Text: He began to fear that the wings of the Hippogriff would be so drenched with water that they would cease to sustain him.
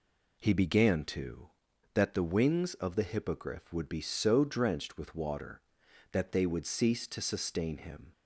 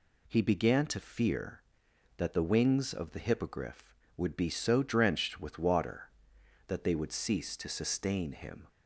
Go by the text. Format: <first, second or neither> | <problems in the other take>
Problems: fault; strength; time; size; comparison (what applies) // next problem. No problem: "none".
second | skips "fear"; at 1.7 s